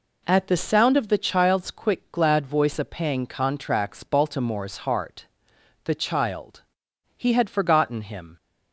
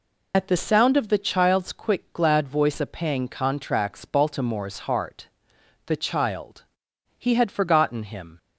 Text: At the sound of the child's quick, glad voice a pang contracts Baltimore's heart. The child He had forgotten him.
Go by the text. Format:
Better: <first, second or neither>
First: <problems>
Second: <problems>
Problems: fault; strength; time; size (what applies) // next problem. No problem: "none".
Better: first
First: pauses between "child" and "He"; noticeable; at 6.6 s; 0.54 s long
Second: loses the start of "At"; at 0.3 s; 95 ms // pauses between "child" and "He"; noticeable; at 6.6 s; 0.54 s long